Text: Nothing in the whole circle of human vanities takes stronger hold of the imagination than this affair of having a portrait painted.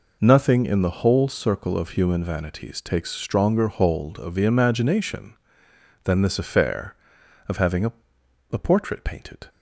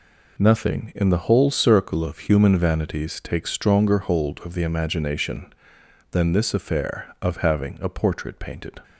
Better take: second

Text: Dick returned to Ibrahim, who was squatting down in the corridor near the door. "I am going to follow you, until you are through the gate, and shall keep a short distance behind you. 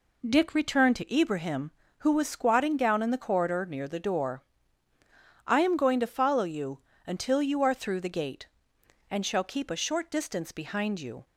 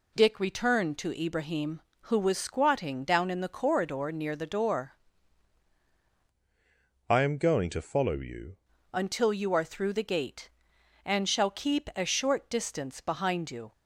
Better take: first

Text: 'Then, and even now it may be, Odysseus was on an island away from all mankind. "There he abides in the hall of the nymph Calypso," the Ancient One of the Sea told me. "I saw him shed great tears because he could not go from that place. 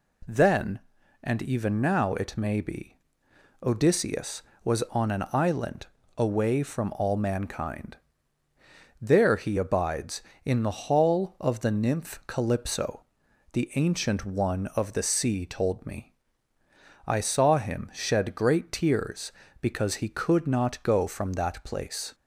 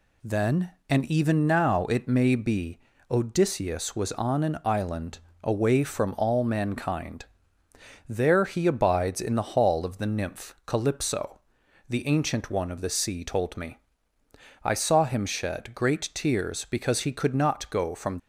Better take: first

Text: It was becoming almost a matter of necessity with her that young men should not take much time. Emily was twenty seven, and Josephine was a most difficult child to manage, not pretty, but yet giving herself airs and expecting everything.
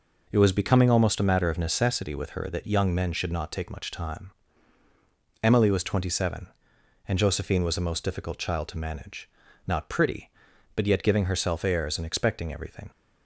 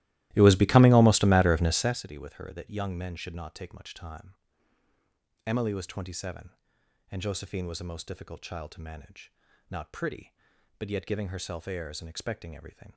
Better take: first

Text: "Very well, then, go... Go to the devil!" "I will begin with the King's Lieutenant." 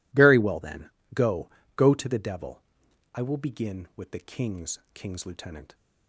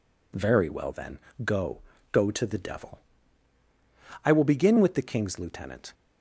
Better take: second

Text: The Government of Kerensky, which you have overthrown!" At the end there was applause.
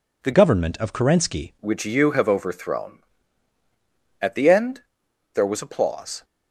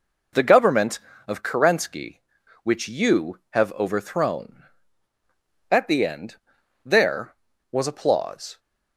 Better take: second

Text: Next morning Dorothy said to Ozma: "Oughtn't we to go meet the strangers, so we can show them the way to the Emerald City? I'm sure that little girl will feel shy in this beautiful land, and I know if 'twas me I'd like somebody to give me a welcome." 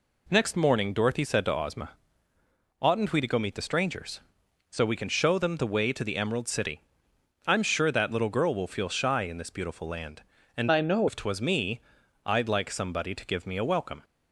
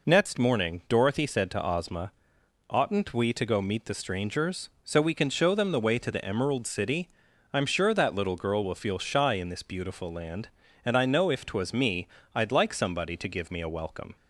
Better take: second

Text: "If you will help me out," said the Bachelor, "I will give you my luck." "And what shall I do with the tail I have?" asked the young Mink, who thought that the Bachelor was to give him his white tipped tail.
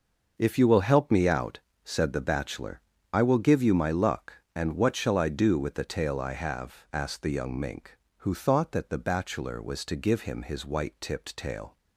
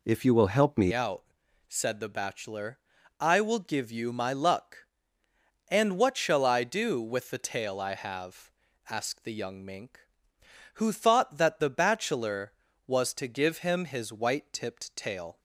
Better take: first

